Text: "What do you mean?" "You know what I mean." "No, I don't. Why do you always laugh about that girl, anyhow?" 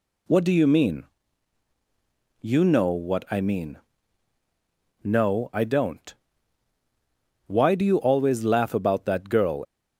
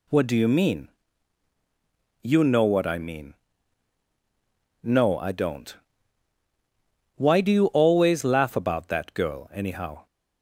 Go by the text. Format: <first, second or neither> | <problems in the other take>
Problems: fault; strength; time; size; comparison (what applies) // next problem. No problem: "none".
second | stops before "anyhow"; at 9.6 s